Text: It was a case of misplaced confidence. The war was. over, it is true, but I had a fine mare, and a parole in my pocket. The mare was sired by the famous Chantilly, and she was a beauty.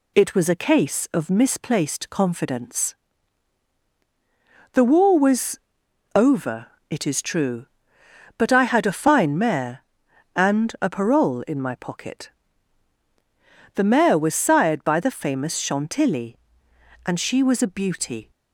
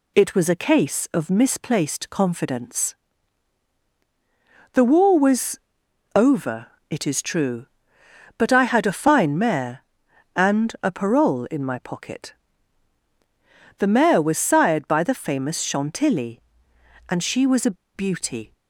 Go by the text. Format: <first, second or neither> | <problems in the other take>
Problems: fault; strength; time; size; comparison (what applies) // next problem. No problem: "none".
first | pauses between "a" and "beauty"; slight; at 17.7 s; 0.21 s long